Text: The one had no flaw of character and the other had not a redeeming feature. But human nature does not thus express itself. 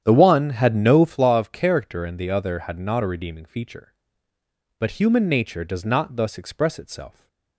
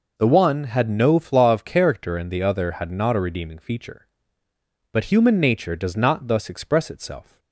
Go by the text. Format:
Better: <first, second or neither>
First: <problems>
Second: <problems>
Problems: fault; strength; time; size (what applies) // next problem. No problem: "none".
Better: second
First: starts louder than the rest; strong; until 1.2 s; 9.5 dB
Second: none